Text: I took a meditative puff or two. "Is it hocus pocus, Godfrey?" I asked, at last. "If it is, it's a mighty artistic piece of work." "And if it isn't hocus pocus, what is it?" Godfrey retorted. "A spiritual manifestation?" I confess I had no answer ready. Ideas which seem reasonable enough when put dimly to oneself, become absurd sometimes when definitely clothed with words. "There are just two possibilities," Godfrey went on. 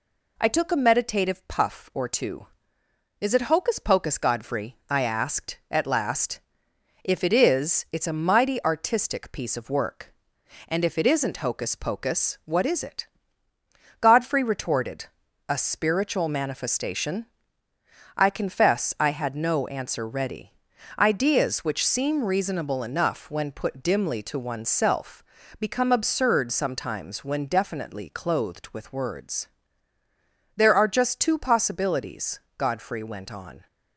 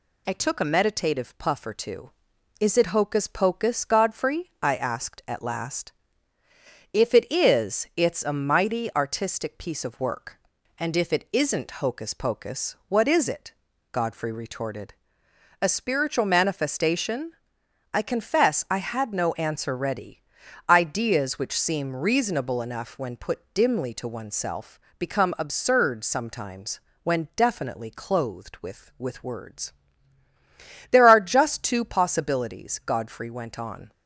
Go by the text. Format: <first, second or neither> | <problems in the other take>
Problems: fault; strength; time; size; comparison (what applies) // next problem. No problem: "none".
first | pauses between "sometimes" and "when"; slight; at 26.7 s; 0.24 s long // says "with" twice; at 28.9 s